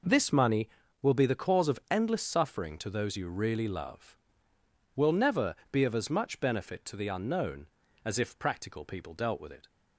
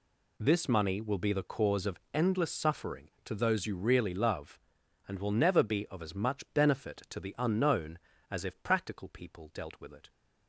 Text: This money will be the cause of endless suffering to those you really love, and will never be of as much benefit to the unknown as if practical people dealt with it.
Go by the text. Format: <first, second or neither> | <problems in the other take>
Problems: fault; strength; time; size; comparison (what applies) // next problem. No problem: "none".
second | skips "and"; at 4.5 s // pauses between "never" and "be"; slight; at 5.5 s; 0.16 s long